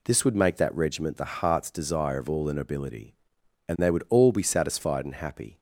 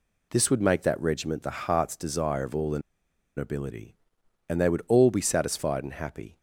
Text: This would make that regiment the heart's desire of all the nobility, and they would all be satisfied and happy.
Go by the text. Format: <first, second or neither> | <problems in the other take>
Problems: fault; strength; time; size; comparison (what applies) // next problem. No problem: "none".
first | pauses between "the" and "nobility"; noticeable; at 2.8 s; 0.56 s long